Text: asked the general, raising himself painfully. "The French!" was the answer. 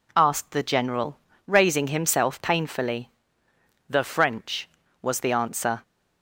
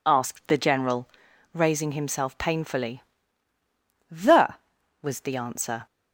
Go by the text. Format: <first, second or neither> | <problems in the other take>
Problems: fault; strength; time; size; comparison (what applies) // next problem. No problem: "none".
first | skips "French"; at 4.7 s